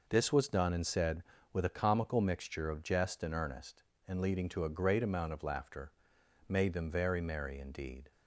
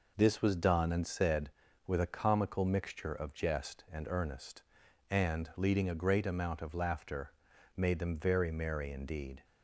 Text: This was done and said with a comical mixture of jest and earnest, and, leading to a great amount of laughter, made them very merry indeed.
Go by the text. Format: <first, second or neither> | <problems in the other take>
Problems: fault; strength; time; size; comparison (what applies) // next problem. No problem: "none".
first | skips "to"; at 5.8 s